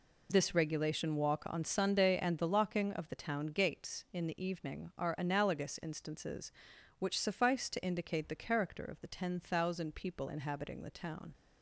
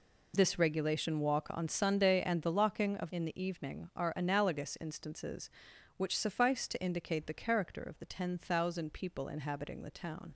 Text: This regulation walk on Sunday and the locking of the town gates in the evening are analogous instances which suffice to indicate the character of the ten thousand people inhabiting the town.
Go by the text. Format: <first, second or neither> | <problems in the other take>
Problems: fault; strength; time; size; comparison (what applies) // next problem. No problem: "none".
first | skips "the town gates"; at 3.1 s